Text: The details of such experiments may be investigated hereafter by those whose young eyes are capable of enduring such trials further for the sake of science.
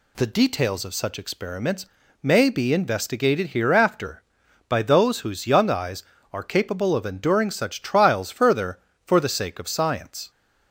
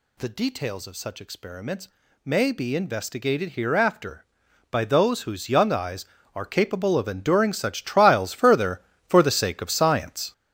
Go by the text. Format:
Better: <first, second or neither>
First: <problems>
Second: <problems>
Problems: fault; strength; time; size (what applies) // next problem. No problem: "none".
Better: first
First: pauses between "experiments" and "may"; at 1.8 s; 0.38 s long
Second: gets louder; strong; throughout; 10 dB // pauses between "experiments" and "may"; at 1.8 s; 0.38 s long